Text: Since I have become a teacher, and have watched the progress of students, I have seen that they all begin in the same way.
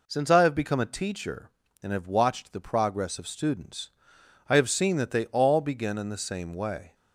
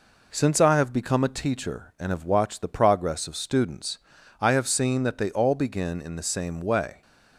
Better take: neither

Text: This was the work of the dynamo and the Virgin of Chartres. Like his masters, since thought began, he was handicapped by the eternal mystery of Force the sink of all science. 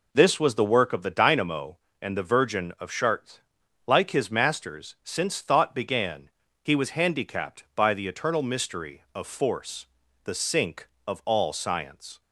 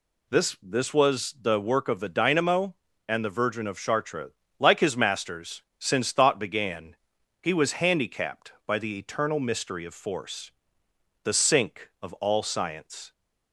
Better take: first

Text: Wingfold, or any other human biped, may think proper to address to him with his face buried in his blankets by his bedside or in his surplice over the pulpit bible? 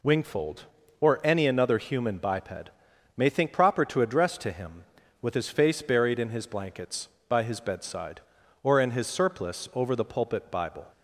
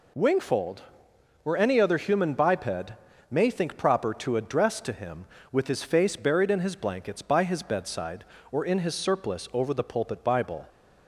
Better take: second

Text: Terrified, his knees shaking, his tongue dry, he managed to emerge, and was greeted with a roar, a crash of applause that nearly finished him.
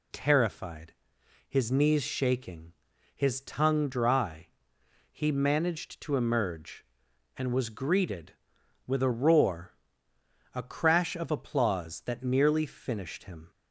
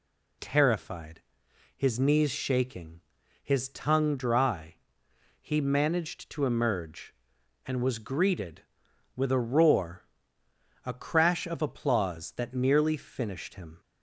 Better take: neither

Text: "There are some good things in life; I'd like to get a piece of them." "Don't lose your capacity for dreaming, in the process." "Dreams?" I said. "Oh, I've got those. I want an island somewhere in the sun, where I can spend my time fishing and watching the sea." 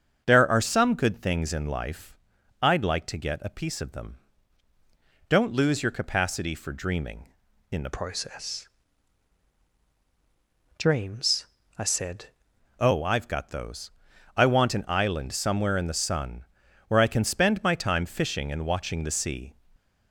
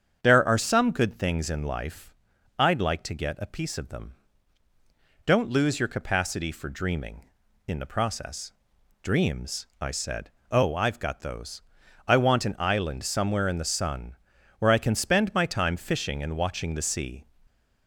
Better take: second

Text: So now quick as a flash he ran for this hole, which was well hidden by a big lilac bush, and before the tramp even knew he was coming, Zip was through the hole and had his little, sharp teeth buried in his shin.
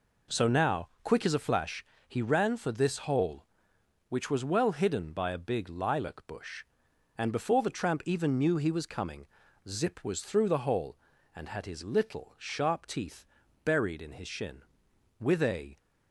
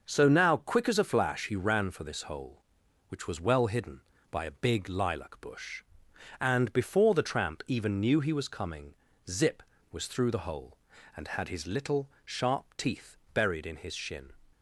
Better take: second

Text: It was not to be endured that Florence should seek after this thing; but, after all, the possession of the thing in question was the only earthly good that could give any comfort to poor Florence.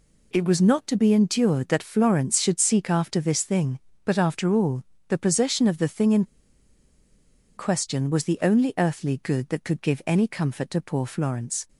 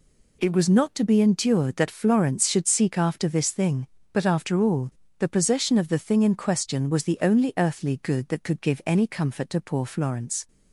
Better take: second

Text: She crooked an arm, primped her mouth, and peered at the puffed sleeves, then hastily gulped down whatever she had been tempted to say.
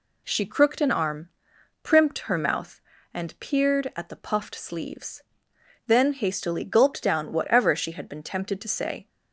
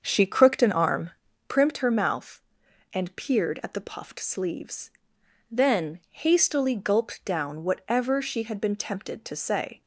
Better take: first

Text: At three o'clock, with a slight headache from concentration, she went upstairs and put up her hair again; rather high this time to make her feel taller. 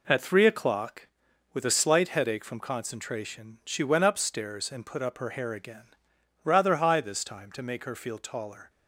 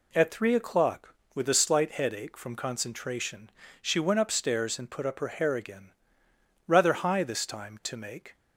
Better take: first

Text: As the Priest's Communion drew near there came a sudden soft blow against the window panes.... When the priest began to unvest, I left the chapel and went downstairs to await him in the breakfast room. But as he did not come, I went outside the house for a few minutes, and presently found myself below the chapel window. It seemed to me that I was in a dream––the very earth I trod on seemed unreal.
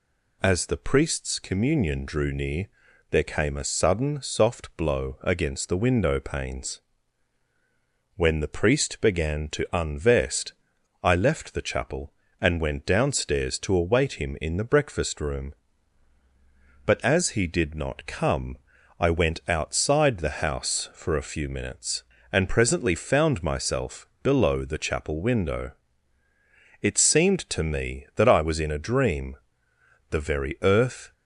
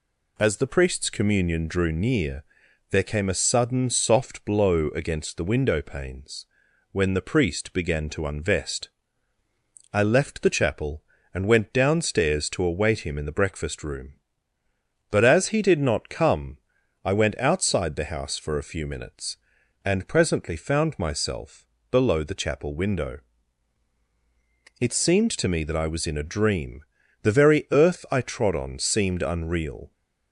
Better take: second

